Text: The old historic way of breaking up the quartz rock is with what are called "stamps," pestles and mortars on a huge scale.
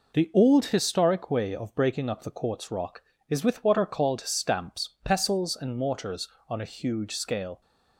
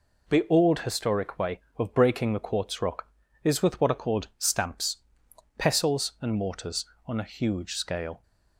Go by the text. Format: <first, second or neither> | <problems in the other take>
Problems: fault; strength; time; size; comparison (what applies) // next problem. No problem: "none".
first | skips "up"; at 2.3 s